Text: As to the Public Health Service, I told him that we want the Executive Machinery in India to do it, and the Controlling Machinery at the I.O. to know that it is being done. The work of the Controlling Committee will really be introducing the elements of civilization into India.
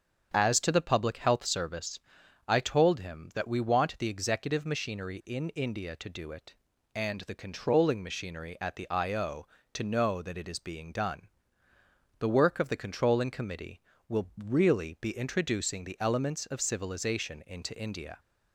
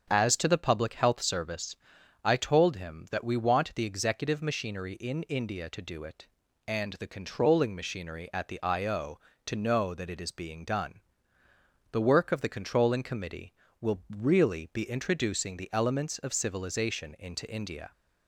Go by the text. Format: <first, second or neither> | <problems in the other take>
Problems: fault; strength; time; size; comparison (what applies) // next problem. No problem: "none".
neither | starts louder than the rest; strong; the same in both